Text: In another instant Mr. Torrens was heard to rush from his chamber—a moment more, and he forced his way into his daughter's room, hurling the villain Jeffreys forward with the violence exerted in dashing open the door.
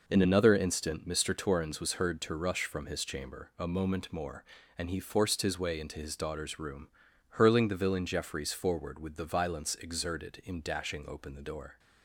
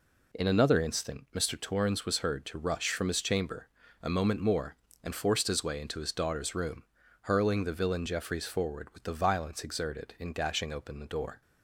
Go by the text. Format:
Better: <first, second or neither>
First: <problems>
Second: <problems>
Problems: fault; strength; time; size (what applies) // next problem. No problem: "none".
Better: first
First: none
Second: skips "he"; at 5.1 s